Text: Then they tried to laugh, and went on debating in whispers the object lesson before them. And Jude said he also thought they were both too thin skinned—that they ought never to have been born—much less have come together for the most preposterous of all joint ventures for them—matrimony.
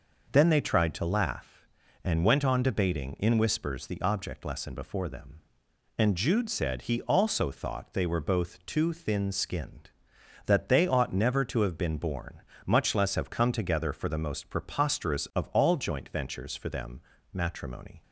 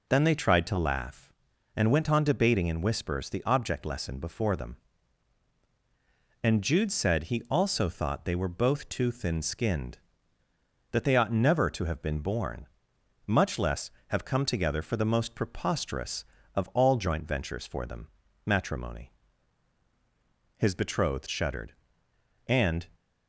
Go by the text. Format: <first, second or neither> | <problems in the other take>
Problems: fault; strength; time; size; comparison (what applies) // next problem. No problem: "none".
first | goes on to say "His betrothed shuddered and"; strong; from 20.5 s on; 2.3 s long